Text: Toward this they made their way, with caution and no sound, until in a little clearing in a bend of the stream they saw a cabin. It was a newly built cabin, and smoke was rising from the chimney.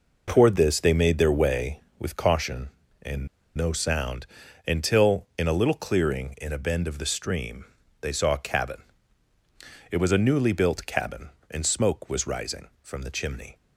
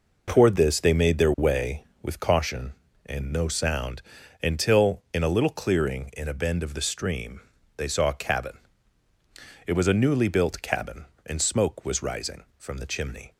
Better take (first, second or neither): second